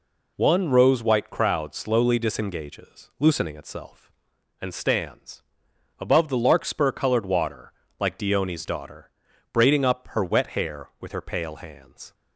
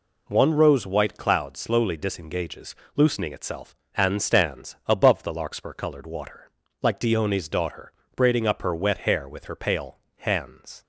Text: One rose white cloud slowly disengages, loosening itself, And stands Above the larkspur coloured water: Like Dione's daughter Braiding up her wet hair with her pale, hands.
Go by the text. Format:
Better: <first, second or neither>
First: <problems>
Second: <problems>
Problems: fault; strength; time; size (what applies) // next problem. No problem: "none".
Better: second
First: says "crowd" for "cloud"; at 1.2 s // pauses between "stands" and "Above"; noticeable; at 5.4 s; 0.58 s long // pauses between "daughter" and "Braiding"; at 9.0 s; 0.42 s long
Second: pauses between "daughter" and "Braiding"; slight; at 7.9 s; 0.24 s long